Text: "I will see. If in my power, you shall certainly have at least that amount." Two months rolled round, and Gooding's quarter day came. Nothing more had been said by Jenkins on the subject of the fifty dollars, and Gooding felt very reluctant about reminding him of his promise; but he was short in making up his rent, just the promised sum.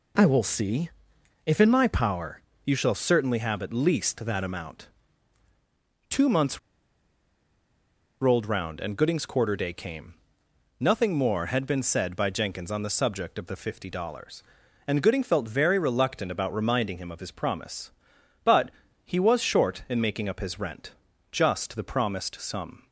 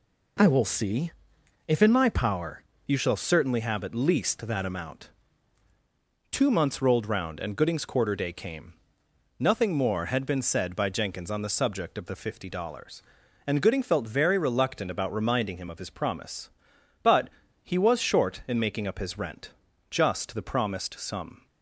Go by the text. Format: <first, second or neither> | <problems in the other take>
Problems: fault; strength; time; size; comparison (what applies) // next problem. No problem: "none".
second | pauses between "months" and "rolled"; strong; at 6.5 s; 1.6 s long // pauses between "but" and "he"; slight; at 18.7 s; 0.32 s long; slight in the second